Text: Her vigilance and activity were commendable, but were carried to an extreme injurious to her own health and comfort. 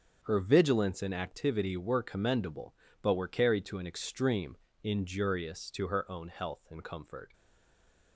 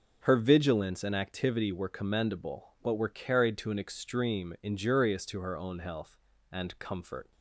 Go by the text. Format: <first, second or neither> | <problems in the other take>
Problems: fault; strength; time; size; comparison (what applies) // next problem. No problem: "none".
second | starts louder than the rest; until 1.2 s; 7 dB // pauses between "extreme" and "injurious"; slight; at 4.5 s; 0.26 s long // stays silent after the last word; slight; from 7.3 s on; 0.8 s long